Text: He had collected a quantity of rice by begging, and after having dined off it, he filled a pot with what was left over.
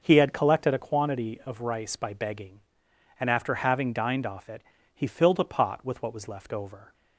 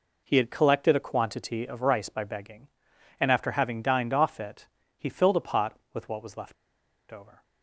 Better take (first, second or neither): first